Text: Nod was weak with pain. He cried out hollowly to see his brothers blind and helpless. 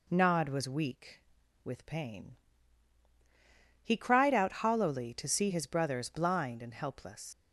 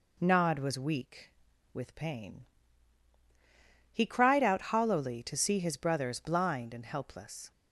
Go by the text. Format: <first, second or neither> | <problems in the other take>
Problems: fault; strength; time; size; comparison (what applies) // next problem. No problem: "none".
second | leaves "helpless" unfinished; at 7.3 s; 65 ms